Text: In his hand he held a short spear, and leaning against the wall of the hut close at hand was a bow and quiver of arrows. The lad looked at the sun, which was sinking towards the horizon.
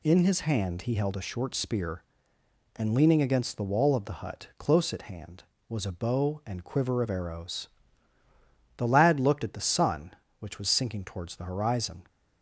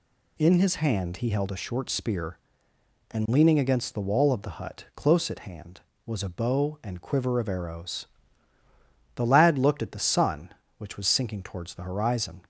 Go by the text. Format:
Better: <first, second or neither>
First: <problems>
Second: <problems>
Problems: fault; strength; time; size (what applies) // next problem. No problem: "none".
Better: neither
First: none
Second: none